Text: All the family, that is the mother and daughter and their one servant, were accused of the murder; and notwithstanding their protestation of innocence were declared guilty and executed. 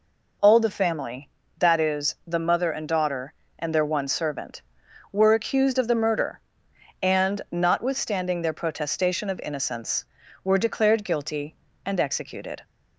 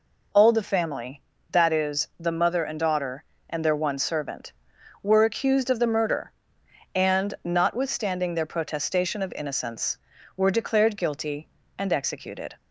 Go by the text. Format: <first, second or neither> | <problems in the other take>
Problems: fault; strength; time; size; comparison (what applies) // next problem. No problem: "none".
neither | none